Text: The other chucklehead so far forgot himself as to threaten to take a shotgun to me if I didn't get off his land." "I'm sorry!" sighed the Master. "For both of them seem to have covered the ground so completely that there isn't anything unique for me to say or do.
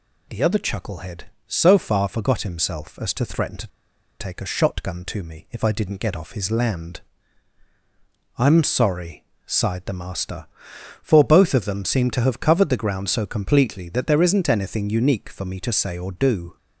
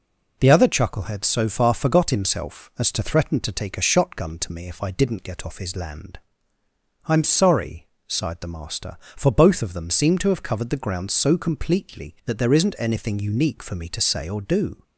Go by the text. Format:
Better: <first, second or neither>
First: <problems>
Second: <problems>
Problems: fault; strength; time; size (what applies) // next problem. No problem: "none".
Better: second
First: pauses between "to" and "take"; noticeable; at 3.6 s; 0.52 s long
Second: none